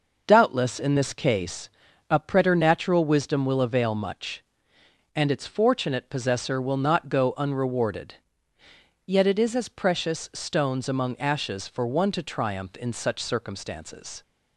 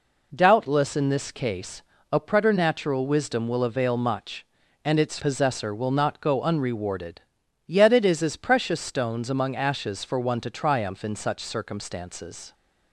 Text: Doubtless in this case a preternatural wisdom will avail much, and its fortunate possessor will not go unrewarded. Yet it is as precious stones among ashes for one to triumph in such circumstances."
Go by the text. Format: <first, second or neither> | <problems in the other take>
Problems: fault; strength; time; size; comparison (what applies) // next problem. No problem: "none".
first | pauses between "case" and "a"; slight; at 1.8 s; 0.30 s long; also in the first // skips "fortunate"; at 5.1 s